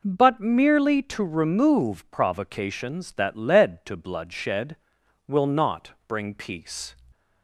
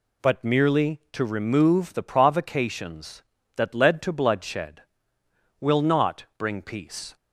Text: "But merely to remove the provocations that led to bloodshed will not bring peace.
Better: second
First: skips "the"; at 2.1 s // pauses between "not" and "bring"; slight; at 5.9 s; 0.18 s long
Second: none

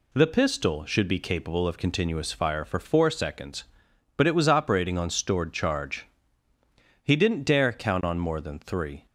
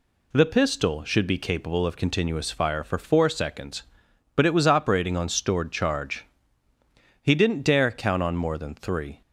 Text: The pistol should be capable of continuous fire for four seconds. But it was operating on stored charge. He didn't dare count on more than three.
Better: neither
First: none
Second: none

